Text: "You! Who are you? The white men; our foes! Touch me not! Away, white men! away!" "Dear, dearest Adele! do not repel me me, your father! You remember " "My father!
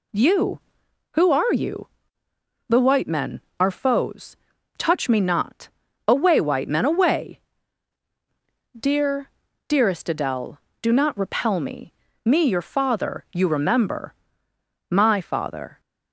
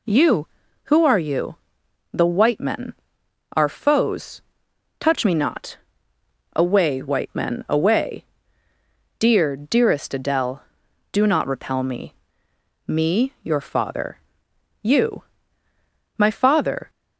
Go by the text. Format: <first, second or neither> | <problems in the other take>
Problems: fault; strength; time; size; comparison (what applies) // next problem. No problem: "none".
first | pauses between "me" and "me"; noticeable; at 12.1 s; 0.72 s long; slight in the first // skips "remember"; at 15.4 s